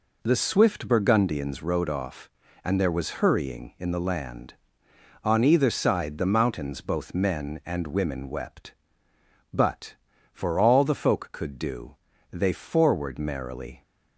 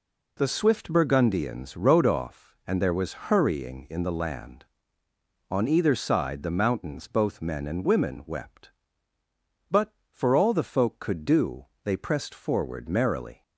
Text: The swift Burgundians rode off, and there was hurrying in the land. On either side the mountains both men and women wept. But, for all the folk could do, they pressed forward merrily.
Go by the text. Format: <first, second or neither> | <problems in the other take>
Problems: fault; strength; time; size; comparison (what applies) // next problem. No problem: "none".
second | skips "pressed"; at 12.5 s